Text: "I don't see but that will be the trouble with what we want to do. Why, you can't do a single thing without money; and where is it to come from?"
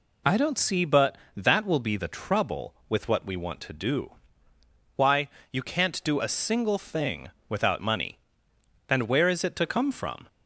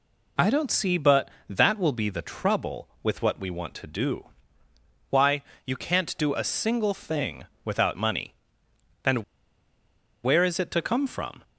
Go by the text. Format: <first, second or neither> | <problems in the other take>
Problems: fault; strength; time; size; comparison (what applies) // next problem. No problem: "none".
first | pauses between "thing" and "without"; slight; at 7.4 s; 0.18 s long; slight in the first // pauses between "and" and "where"; at 9.2 s; 0.99 s long